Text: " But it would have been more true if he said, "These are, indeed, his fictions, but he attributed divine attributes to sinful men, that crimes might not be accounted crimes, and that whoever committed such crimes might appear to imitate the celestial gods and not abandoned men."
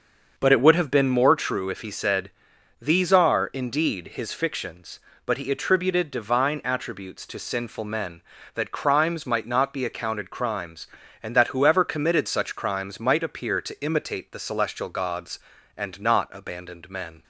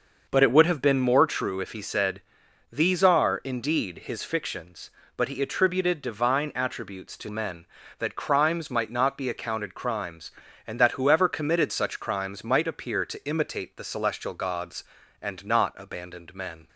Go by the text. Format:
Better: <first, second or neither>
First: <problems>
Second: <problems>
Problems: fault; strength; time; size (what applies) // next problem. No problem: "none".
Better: first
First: starts louder than the rest; until 1.3 s; 6.5 dB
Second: starts louder than the rest; noticeable; until 1.2 s; 6 dB // skips "sinful"; at 7.2 s